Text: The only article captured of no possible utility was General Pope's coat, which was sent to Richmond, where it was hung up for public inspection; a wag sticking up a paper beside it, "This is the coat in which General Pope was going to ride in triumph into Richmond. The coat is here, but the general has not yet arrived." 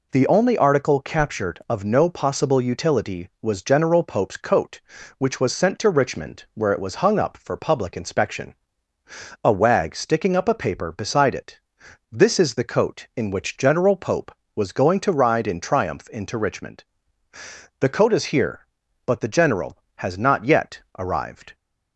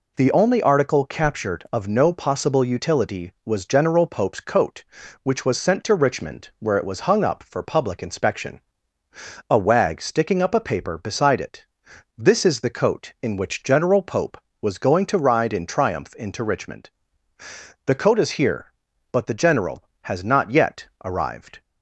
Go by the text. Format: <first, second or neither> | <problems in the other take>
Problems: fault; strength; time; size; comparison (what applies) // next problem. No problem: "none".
neither | none